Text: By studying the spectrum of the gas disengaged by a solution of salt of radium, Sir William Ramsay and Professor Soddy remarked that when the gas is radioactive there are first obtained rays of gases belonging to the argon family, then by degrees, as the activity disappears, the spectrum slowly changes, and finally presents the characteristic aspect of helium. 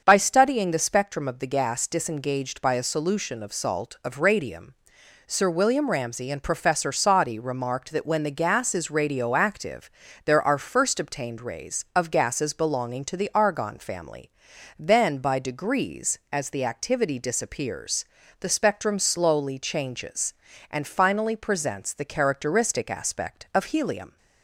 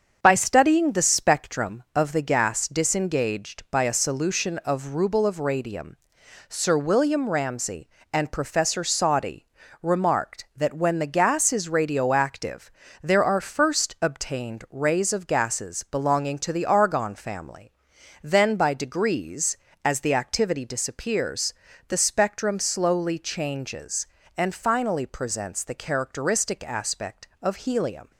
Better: first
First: starts louder than the rest; until 1.0 s; 6.5 dB // pauses between "radioactive" and "there"; slight; at 9.8 s; 0.36 s long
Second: starts louder than the rest; until 1.2 s; 7 dB // says "ruble" for "salt"; at 4.9 s // pauses between "Soddy" and "remarked"; slight; at 9.4 s; 0.34 s long // pauses between "radioactive" and "there"; slight; at 12.7 s; 0.32 s long

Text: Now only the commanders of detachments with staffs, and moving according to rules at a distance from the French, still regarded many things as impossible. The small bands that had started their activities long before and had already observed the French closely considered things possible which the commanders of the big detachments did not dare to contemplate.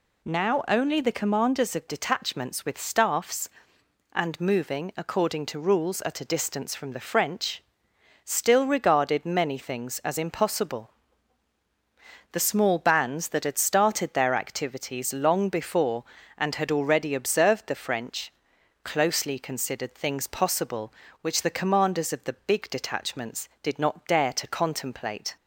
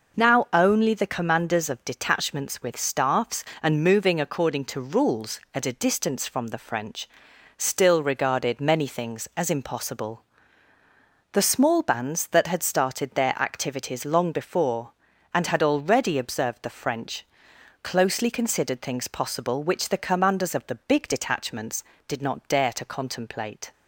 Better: neither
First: pauses between "French" and "closely"; noticeable; at 18.3 s; 0.52 s long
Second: pauses between "French" and "closely"; noticeable; at 17.2 s; 0.58 s long

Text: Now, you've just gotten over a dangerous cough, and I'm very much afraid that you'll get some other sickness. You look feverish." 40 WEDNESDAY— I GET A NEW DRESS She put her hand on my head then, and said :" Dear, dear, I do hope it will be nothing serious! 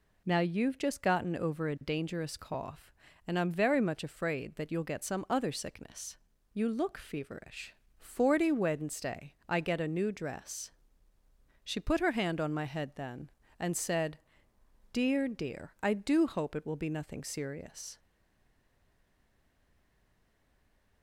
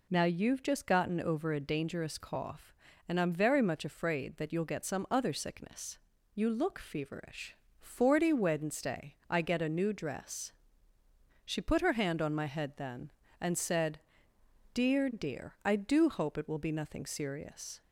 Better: second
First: pauses between "DRESS" and "She"; noticeable; at 10.7 s; 0.94 s long // stays silent after the last word; strong; from 17.9 s on; 3.1 s long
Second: pauses between "DRESS" and "She"; noticeable; at 10.5 s; 0.94 s long

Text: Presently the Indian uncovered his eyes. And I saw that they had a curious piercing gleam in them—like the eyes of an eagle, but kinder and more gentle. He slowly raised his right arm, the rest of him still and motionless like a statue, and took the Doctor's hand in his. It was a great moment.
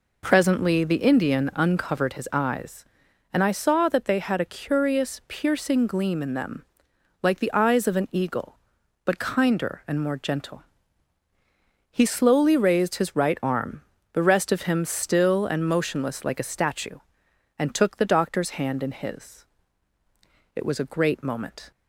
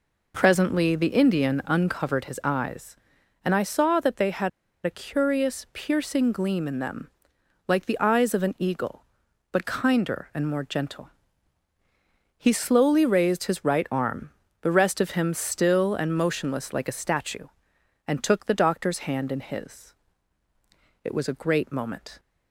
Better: first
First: none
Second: pauses between "had" and "a"; slight; at 4.4 s; 0.35 s long

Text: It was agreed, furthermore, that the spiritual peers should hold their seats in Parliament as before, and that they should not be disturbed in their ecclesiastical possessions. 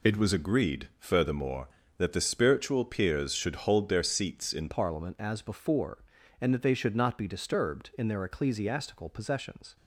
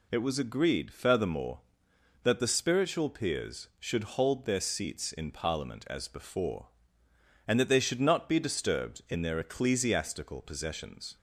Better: second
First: changes voice at "Parliament"; from 4.7 s on; 5.0 s long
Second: none

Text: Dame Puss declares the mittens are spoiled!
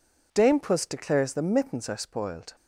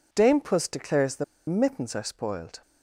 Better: first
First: none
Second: pauses between "the" and "mittens"; slight; at 1.2 s; 0.22 s long

